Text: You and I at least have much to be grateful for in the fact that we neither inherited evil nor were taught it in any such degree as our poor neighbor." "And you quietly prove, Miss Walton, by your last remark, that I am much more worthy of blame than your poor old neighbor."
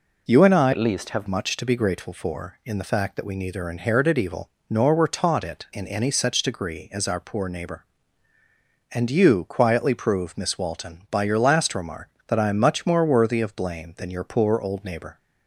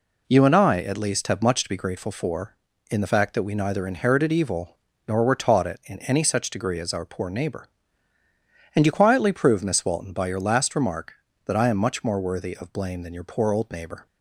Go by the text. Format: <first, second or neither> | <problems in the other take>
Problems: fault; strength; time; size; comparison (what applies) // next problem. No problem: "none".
second | changes voice from "at" to "have"; from 0.7 to 1.2 s; 0.5 s long // pauses between "evil" and "nor"; slight; at 4.4 s; 0.22 s long; slight in the second